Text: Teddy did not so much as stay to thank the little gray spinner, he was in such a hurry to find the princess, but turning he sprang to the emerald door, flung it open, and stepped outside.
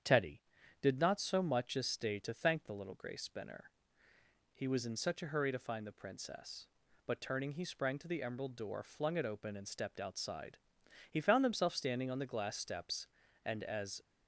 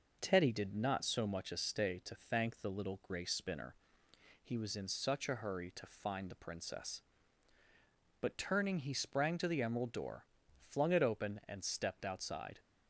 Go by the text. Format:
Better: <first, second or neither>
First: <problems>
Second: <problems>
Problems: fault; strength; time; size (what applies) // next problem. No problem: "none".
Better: second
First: starts louder than the rest; strong; until 1.4 s; 8.5 dB // goes on to say "He found himself standing on the glass steps and as"; strong; from 11.0 s on; 2.9 s long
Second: none